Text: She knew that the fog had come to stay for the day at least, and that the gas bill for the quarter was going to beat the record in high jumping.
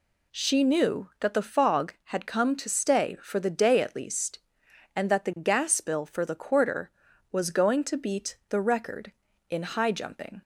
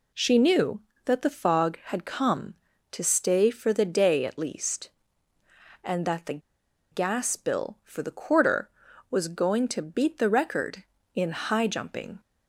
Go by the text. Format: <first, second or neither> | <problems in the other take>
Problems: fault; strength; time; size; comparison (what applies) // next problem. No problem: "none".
first | pauses between "the" and "gas"; noticeable; at 6.3 s; 0.52 s long